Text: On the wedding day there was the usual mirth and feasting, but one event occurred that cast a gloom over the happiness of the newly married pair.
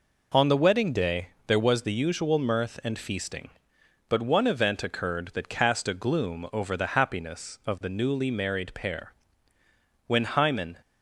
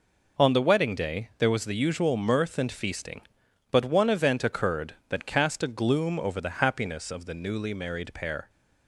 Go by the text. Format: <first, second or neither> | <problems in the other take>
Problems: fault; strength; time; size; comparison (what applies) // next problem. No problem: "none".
second | pauses between "day" and "there"; slight; at 1.2 s; 0.20 s long // goes on to say "When Hymen"; noticeable; from 10.0 s on; 0.72 s long